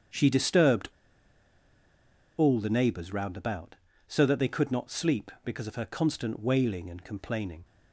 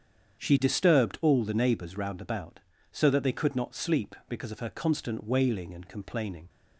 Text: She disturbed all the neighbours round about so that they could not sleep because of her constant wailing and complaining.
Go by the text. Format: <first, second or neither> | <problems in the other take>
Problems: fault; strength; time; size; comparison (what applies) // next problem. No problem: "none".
second | starts louder than the rest; strong; until 2.6 s; 8 dB; strong in the second // pauses between "disturbed" and "all"; strong; at 0.9 s; 1.4 s long